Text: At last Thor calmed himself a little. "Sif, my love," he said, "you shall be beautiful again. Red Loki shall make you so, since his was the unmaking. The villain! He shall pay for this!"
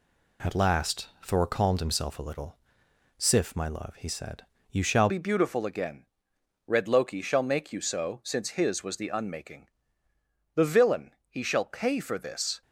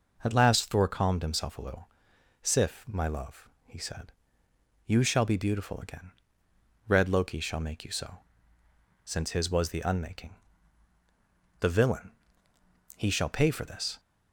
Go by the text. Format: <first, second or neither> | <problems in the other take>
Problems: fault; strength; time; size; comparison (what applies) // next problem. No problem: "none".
second | changes voice at "be"; from 5.0 s on; 7.6 s long